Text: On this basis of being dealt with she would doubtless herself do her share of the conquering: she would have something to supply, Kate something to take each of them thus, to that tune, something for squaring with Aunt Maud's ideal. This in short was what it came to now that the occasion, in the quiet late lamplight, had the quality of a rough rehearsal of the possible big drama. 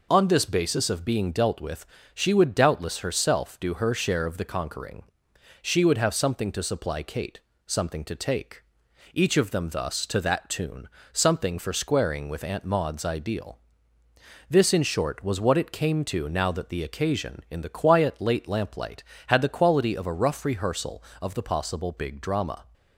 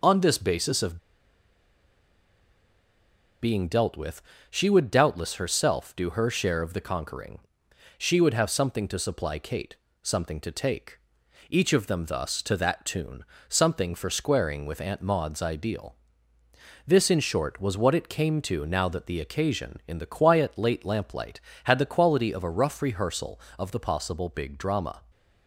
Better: first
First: pauses between "with" and "she"; slight; at 1.8 s; 0.28 s long // pauses between "Kate" and "something"; slight; at 7.4 s; 0.24 s long // pauses between "take" and "each"; noticeable; at 8.6 s; 0.50 s long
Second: pauses between "of" and "being"; strong; at 0.9 s; 2.4 s long // pauses between "with" and "she"; slight; at 4.2 s; 0.28 s long // pauses between "Kate" and "something"; slight; at 9.7 s; 0.24 s long // pauses between "take" and "each"; noticeable; at 10.9 s; 0.50 s long

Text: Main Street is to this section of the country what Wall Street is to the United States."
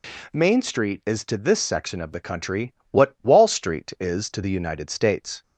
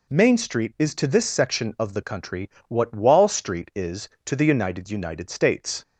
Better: first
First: pauses between "country" and "what"; slight; at 2.7 s; 0.16 s long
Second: pauses between "country" and "what"; slight; at 2.4 s; 0.22 s long // says "United" twice; at 4.8 s

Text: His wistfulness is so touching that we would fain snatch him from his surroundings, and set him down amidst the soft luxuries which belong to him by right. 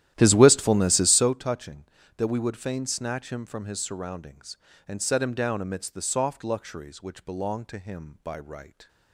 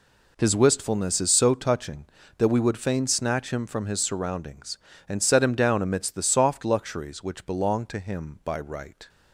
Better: second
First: starts louder than the rest; strong; until 1.4 s; 12.5 dB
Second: none

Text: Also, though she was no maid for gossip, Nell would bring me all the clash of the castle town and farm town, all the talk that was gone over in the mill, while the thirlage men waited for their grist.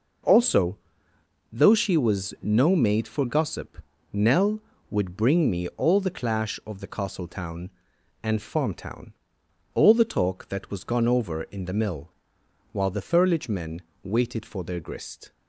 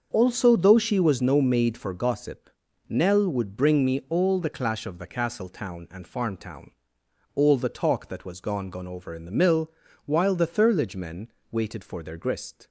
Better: first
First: pauses between "men" and "waited"; slight; at 13.8 s; 0.22 s long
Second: starts louder than the rest; until 1.1 s; 6.5 dB // says "gone" twice; at 8.6 s // pauses between "men" and "waited"; slight; at 11.2 s; 0.22 s long

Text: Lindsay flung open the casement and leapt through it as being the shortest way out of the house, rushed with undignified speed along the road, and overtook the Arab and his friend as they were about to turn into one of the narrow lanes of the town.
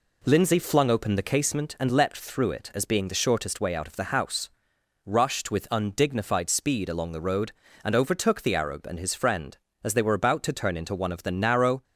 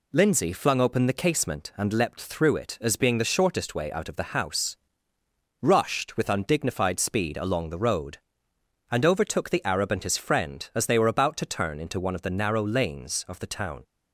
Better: second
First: stops before "lanes of the town"; at 11.8 s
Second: none

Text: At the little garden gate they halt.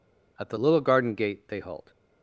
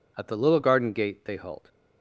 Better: neither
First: none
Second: none

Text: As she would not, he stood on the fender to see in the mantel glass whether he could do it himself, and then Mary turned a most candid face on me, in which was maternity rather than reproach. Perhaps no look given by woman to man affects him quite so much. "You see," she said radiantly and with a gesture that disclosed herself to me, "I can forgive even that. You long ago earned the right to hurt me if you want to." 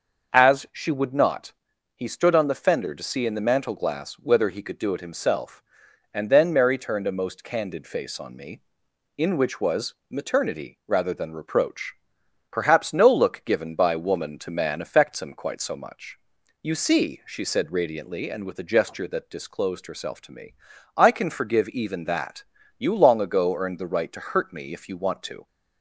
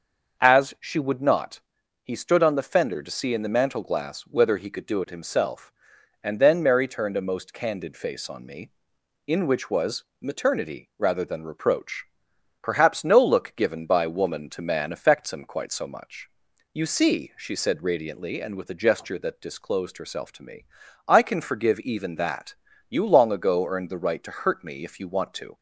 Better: neither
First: starts louder than the rest; until 1.3 s; 6.5 dB // pauses between "was" and "maternity"; slight; at 9.9 s; 0.16 s long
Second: starts louder than the rest; until 1.4 s; 6.5 dB // pauses between "was" and "maternity"; slight; at 10.0 s; 0.18 s long

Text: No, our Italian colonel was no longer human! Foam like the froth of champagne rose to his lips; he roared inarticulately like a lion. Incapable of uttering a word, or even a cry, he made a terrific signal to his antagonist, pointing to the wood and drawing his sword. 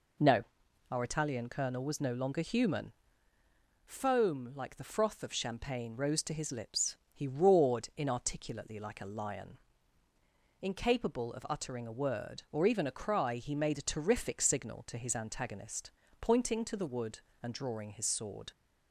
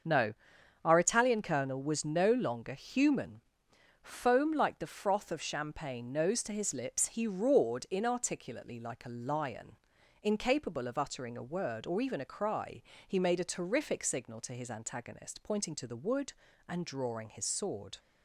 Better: first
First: none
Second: starts louder than the rest; until 1.5 s; 6.5 dB // says "nose" for "rose"; at 6.1 s

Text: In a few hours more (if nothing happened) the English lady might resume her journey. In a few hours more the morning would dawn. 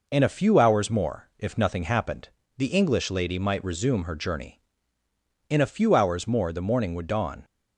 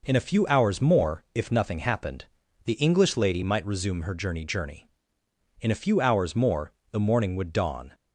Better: first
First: none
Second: says "journey" twice; at 4.4 s // pauses between "more" and "the"; slight; at 6.7 s; 0.18 s long

